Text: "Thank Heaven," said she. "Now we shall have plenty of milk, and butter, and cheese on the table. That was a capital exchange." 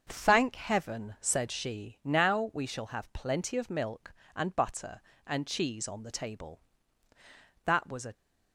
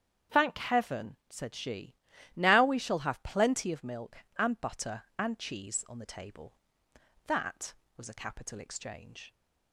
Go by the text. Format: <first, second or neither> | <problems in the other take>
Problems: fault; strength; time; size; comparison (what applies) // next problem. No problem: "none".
second | starts louder than the rest; until 1.1 s; 6.5 dB; strong in the second // stops before "capital exchange"; at 8.1 s